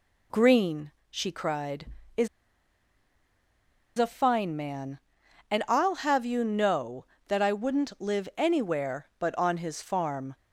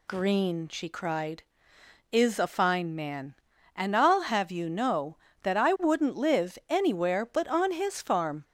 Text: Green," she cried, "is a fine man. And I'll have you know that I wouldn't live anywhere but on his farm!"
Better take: second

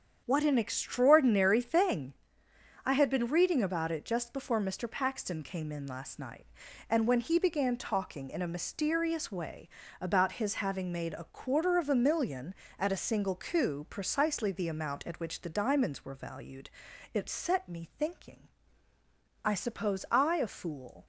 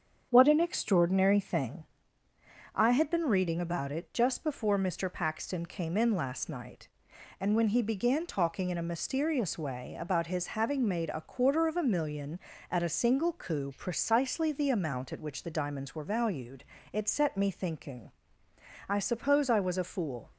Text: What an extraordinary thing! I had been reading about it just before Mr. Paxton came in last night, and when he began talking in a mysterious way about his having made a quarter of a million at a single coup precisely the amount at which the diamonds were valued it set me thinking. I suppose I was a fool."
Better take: second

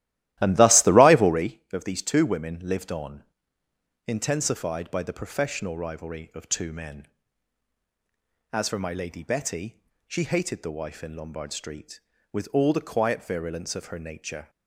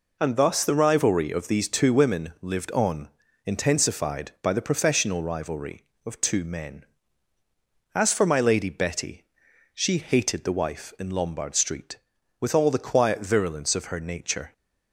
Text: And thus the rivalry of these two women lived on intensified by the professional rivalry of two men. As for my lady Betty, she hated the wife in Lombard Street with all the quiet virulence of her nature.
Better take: second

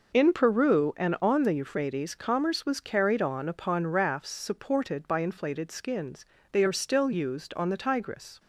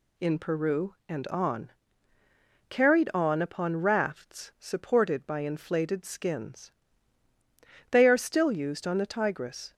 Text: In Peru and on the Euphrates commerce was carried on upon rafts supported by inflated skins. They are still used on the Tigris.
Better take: first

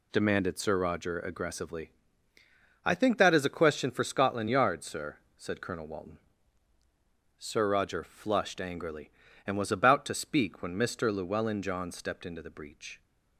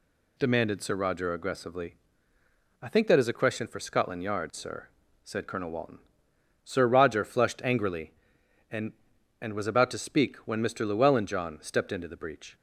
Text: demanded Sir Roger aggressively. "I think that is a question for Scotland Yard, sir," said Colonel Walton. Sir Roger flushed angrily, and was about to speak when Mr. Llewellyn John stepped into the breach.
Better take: first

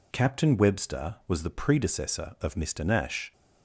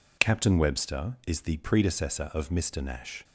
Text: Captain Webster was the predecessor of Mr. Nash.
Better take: first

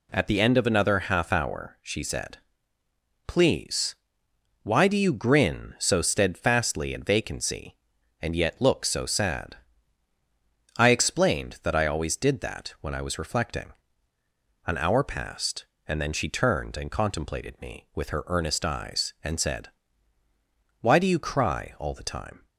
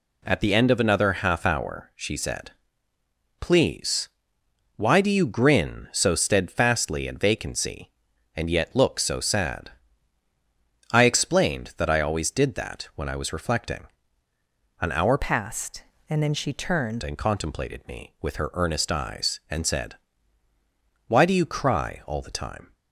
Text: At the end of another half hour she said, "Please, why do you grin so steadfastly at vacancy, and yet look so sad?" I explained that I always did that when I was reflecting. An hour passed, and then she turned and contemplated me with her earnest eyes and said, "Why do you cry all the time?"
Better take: first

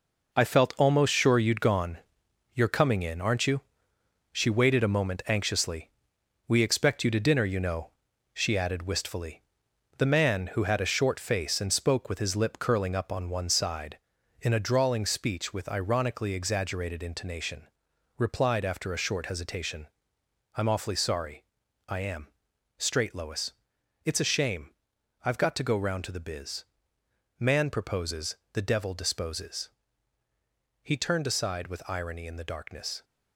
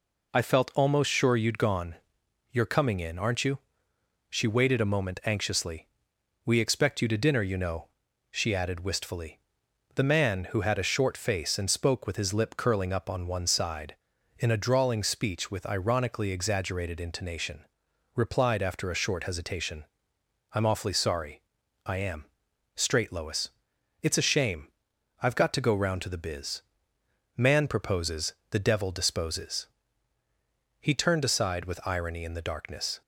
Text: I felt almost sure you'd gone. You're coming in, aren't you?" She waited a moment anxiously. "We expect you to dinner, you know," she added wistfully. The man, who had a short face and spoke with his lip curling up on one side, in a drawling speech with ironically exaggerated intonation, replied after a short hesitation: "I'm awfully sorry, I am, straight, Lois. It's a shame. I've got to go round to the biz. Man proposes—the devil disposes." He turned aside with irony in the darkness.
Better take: second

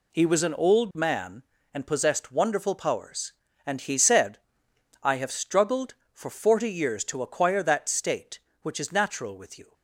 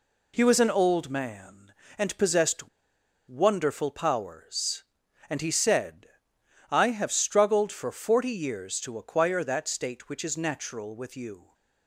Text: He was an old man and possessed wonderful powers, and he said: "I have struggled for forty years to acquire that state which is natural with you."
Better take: first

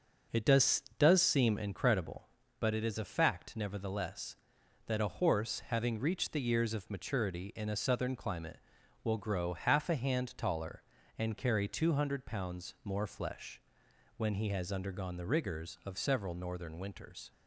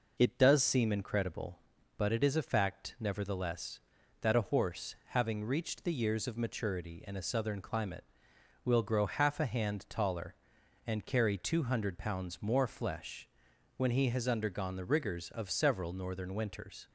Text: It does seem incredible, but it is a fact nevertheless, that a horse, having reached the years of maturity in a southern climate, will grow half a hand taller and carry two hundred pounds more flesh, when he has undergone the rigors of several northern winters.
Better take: second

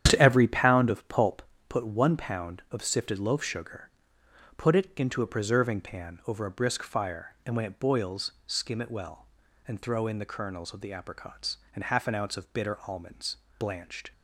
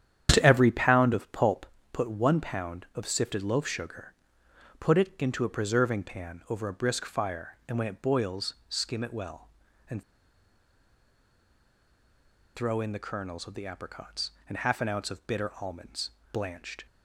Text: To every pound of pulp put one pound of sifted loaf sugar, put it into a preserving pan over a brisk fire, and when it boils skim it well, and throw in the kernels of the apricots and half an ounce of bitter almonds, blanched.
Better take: first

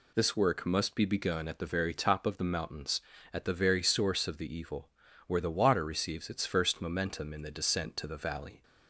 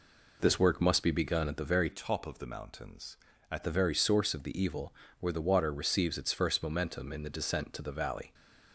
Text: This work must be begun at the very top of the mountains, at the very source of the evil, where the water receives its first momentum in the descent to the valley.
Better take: first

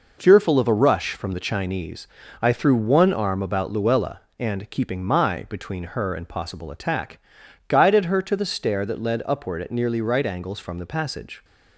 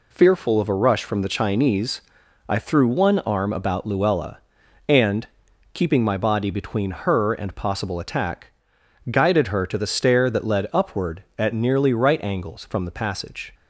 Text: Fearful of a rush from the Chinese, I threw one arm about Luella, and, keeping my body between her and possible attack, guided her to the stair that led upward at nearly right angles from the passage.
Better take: second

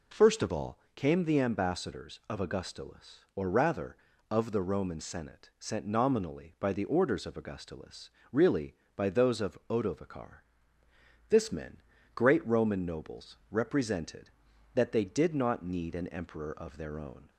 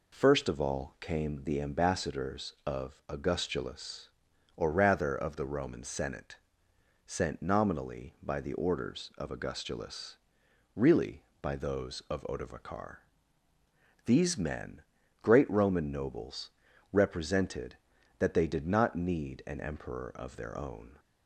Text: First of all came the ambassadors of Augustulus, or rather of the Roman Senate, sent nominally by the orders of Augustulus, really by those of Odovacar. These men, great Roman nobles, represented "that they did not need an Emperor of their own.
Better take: second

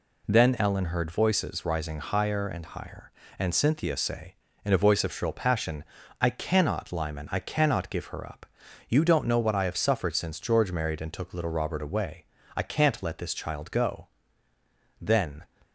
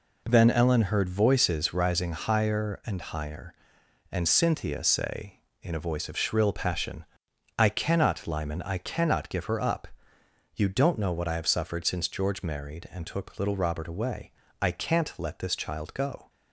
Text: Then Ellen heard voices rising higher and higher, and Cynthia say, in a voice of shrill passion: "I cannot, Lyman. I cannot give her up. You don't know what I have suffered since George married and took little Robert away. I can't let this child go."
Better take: second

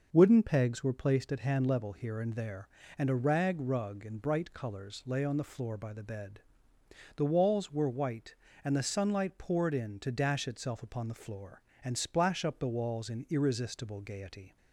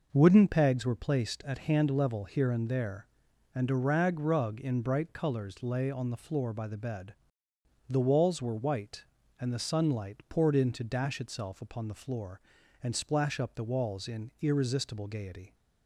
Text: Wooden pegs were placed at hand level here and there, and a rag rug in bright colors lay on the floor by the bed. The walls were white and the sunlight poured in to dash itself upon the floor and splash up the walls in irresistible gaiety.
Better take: neither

